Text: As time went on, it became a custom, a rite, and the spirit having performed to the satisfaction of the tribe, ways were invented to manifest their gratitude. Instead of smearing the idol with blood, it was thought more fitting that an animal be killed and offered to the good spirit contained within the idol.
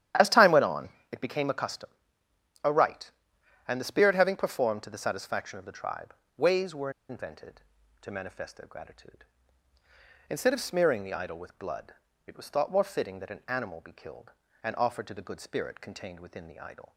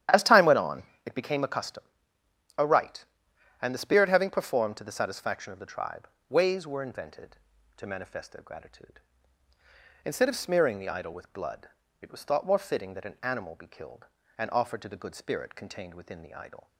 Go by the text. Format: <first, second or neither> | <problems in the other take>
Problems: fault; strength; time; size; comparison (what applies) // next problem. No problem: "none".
second | starts louder than the rest; strong; until 1.4 s; 11.5 dB; strong in the second // pauses between "were" and "invented"; slight; at 6.8 s; 0.19 s long